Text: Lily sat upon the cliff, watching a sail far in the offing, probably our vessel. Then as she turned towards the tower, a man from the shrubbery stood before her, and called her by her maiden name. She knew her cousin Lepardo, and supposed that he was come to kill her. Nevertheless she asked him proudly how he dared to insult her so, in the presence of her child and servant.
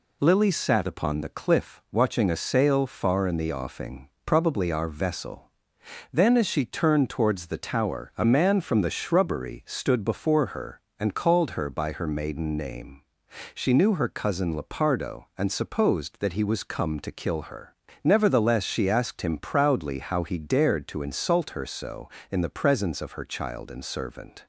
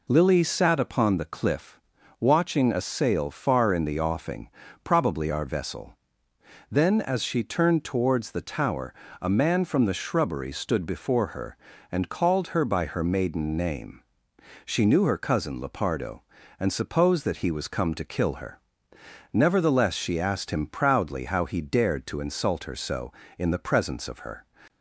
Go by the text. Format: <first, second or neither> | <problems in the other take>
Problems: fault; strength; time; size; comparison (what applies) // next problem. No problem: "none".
first | stops before "child and servant"; at 24.6 s